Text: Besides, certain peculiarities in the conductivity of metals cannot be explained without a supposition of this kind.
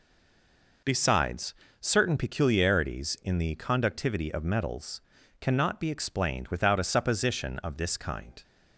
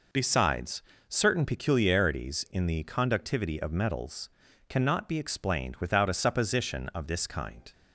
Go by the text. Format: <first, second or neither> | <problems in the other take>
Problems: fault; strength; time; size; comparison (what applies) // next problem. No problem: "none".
second | stays silent before the first word; slight; until 0.8 s; 0.8 s long // pauses between "metals" and "cannot"; at 4.9 s; 0.40 s long; also in the second